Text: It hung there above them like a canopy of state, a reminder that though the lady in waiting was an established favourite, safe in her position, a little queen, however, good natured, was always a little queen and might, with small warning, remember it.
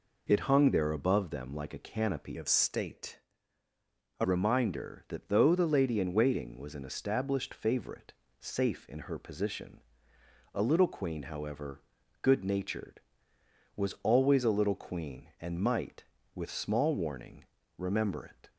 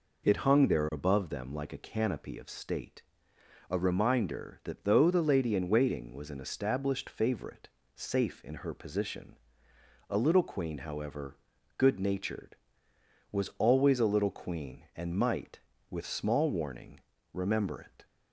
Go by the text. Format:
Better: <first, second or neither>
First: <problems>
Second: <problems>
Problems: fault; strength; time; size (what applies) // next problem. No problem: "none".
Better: second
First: changes voice from "of" to "a"; from 2.3 to 4.2 s; 1.9 s long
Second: none